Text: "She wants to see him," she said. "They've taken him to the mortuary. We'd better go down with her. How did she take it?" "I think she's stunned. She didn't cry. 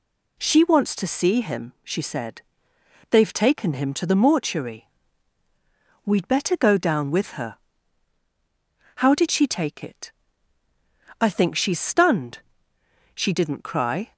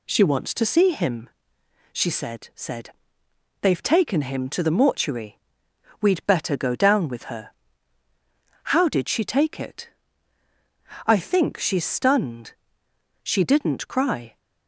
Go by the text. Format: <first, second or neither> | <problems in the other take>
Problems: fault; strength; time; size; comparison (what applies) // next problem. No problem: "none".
first | says "said" twice; at 2.5 s